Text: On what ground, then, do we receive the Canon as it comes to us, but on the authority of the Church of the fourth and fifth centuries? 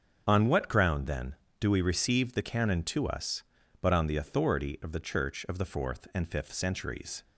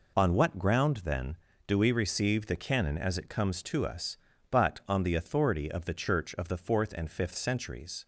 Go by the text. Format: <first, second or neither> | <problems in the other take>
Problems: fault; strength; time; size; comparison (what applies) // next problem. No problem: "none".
second | starts louder than the rest; strong; until 1.2 s; 7.5 dB // skips "as it comes"; at 2.8 s